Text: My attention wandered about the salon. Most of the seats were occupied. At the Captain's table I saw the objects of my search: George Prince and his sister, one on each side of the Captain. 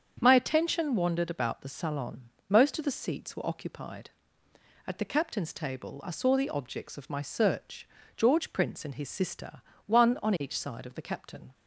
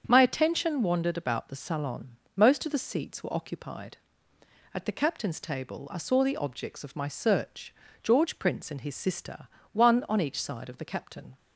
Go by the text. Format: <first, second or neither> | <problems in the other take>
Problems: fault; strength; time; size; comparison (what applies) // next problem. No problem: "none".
neither | starts louder than the rest; strong; the same in both